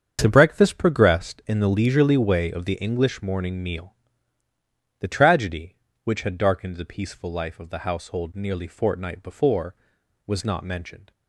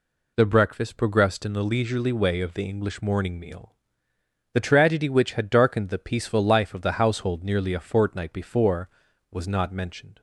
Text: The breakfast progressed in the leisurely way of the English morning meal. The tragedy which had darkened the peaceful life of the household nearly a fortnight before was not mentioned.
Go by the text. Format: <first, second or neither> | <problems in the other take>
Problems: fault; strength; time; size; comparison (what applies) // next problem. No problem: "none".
second | starts louder than the rest; strong; until 1.2 s; 7.5 dB // skips "a"; at 8.6 s